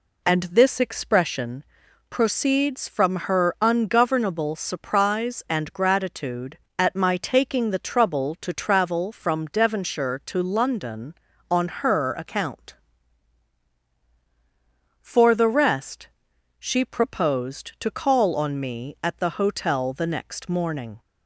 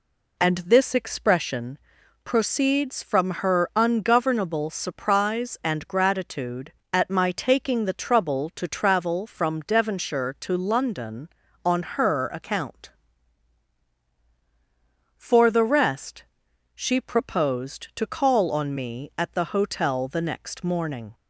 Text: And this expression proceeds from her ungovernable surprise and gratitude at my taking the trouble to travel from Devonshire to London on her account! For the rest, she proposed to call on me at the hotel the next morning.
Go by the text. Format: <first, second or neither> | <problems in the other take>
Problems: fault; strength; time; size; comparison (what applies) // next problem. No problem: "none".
neither | pauses between "expression" and "proceeds"; noticeable; the same in both